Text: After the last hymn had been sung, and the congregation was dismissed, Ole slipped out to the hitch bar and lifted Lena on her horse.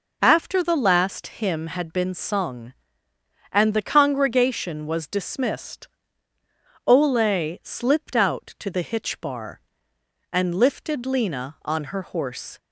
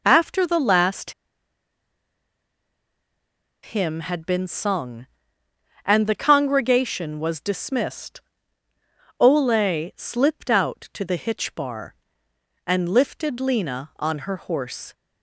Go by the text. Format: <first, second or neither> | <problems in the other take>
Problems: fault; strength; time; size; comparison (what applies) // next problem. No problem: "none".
first | pauses between "last" and "hymn"; strong; at 1.1 s; 2.5 s long